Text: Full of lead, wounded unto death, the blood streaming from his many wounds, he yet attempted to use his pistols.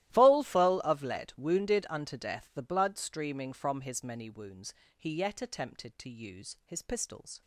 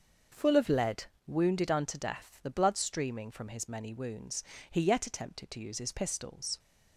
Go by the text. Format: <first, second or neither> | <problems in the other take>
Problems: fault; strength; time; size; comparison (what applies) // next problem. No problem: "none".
second | starts louder than the rest; strong; until 1.1 s; 14.5 dB; also in the second // says "Full" twice; at 0.4 s